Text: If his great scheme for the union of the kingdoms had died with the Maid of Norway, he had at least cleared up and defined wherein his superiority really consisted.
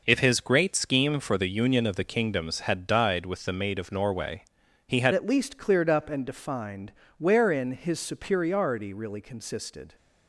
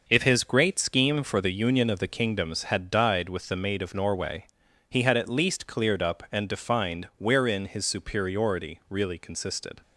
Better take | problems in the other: second | changes voice at "at"; from 5.1 s on; 4.8 s long // pauses between "defined" and "wherein"; slight; at 6.9 s; 0.26 s long

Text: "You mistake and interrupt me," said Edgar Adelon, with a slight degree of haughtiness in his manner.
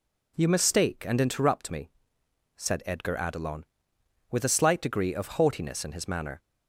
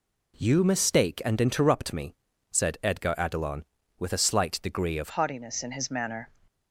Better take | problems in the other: first | changes voice at "haughtiness"; from 5.1 s on; 1.2 s long

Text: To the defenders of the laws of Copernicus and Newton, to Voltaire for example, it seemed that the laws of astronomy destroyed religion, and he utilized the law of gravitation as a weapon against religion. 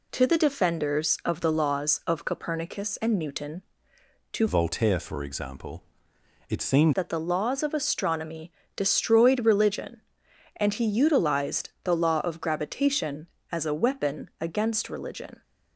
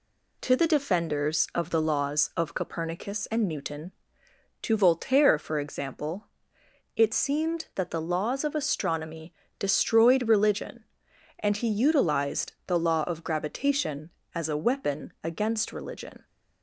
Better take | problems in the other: second | changes voice from "Voltaire" to "seemed"; from 4.4 to 6.9 s; 2.5 s long // pauses between "astronomy" and "destroyed"; slight; at 8.5 s; 0.24 s long; slight in the second

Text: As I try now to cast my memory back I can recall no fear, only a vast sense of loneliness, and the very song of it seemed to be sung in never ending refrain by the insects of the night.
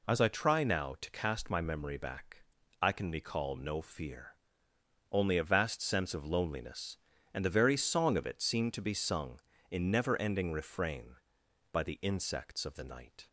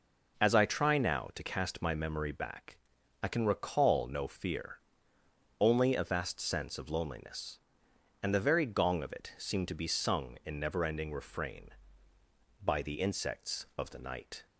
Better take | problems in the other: first | pauses between "back" and "I"; noticeable; at 2.7 s; 0.48 s long; also in the first // says "gong" for "song"; at 8.6 s

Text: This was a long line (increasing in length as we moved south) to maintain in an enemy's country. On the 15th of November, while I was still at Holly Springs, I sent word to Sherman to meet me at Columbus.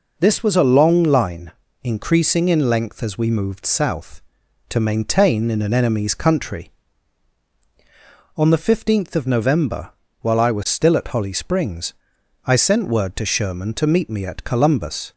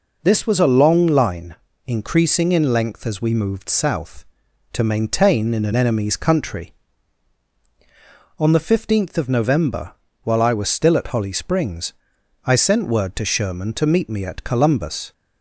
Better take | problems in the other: neither | none

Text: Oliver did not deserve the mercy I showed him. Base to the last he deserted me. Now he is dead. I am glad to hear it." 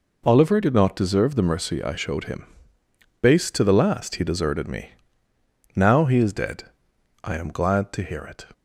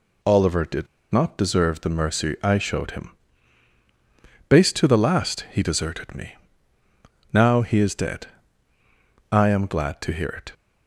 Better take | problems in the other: first | pauses between "did" and "not"; slight; at 0.8 s; 0.25 s long

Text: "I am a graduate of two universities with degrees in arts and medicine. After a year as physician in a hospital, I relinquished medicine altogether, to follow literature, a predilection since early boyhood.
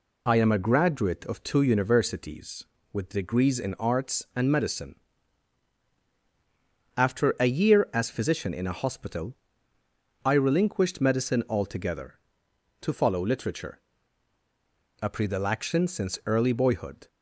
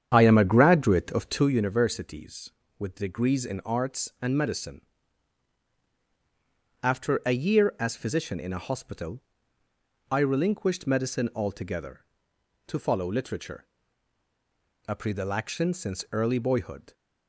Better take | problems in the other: first | starts louder than the rest; strong; until 1.5 s; 8.5 dB

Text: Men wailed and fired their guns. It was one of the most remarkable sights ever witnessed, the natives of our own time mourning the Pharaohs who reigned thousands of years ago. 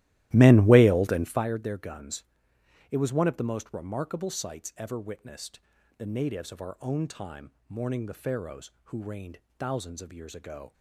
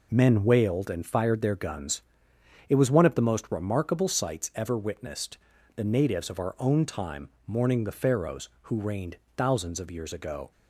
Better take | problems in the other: second | starts louder than the rest; strong; until 1.5 s; 15.5 dB // pauses between "time" and "mourning"; slight; at 7.5 s; 0.18 s long; slight in the second // pauses between "reigned" and "thousands"; slight; at 9.3 s; 0.20 s long; slight in the second

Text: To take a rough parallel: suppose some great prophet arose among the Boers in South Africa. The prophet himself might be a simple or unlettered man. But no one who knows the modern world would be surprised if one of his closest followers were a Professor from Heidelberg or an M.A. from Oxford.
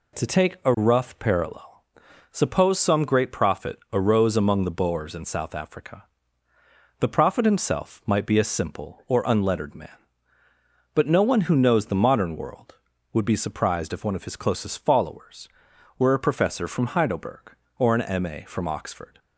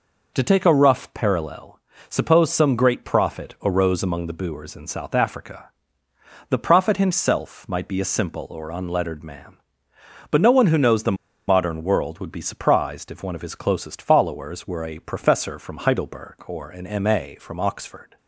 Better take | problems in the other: first | pauses between "the" and "modern"; slight; at 11.1 s; 0.33 s long

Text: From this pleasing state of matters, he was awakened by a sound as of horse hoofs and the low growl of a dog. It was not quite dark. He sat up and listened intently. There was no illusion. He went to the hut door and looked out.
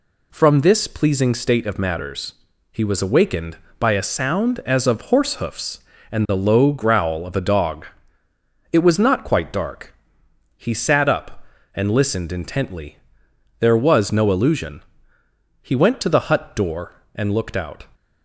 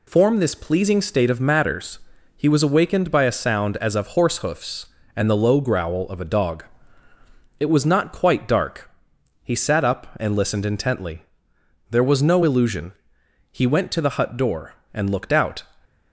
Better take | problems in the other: first | says "Form" for "From"; at 0.0 s

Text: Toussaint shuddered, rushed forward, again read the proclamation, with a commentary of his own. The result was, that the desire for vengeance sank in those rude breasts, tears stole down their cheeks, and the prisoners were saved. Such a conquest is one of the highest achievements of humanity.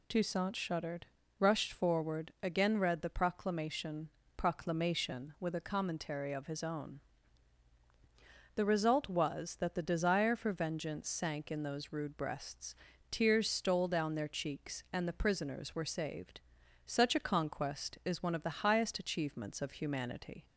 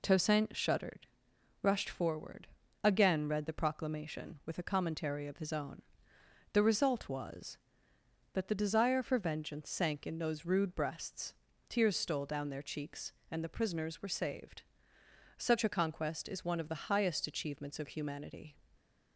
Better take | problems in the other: second | says "proclamation" twice; at 4.3 s

